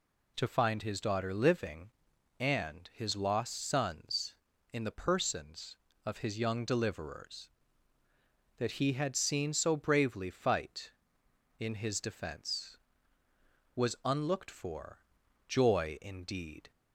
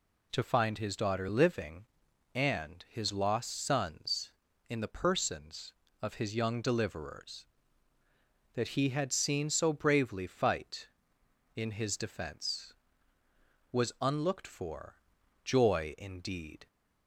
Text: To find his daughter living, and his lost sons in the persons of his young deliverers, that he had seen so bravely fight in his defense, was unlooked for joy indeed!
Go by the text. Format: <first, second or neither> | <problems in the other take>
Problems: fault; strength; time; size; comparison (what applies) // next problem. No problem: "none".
neither | pauses between "for" and "joy"; noticeable; the same in both